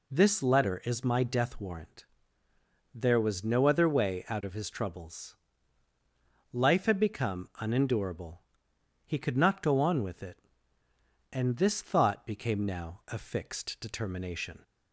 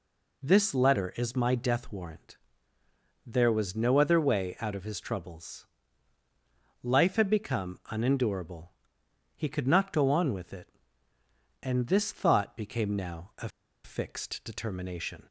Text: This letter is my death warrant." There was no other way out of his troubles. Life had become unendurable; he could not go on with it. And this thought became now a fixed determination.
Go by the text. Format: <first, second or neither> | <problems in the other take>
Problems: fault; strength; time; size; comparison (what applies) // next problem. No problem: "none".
first | pauses between "a" and "fixed"; slight; at 13.4 s; 0.35 s long